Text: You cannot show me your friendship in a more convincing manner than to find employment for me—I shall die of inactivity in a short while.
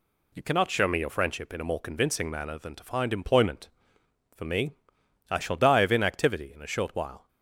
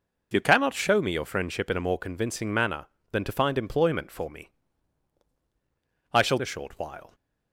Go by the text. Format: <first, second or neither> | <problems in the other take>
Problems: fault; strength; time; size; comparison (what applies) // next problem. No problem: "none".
first | skips "die of inactivity in"; at 6.3 s